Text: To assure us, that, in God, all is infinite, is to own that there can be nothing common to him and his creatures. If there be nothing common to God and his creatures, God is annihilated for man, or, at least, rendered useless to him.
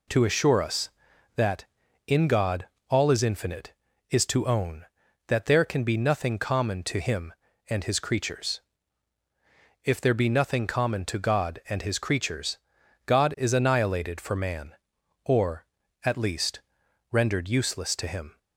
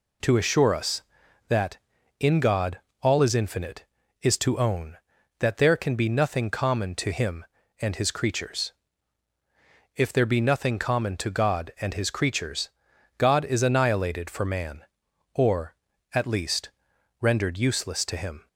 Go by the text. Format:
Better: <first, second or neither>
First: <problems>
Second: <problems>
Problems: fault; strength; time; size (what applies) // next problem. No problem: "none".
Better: neither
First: none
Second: none